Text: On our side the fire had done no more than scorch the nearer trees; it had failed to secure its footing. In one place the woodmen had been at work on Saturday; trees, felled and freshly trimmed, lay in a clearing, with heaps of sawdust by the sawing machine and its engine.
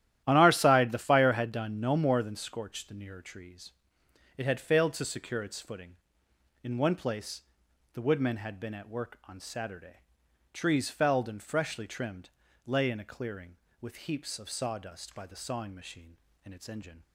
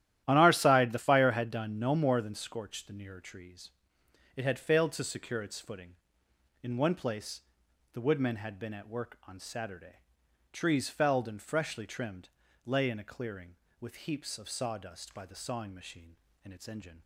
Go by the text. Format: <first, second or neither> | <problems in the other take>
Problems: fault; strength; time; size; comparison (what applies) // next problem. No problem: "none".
neither | starts louder than the rest; strong; the same in both // pauses between "place" and "the"; noticeable; the same in both